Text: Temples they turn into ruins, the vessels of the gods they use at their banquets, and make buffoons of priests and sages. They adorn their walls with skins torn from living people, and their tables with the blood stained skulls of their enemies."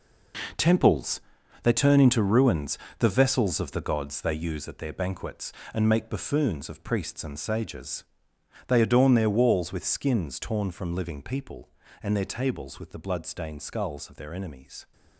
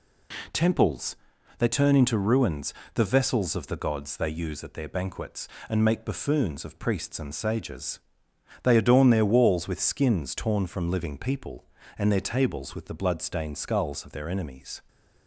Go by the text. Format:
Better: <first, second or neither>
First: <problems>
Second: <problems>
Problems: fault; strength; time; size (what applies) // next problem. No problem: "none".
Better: second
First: gets quieter; strong; throughout; 10 dB // pauses between "Temples" and "they"; at 1.2 s; 0.40 s long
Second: pauses between "Temples" and "they"; at 1.1 s; 0.40 s long